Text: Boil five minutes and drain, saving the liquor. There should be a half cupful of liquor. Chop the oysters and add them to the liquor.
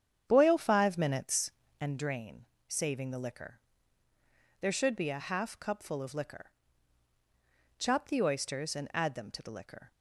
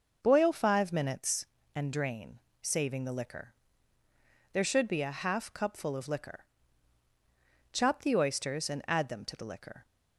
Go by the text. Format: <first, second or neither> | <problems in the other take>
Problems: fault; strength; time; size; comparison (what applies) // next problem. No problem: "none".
second | starts louder than the rest; strong; until 2.0 s; 8.5 dB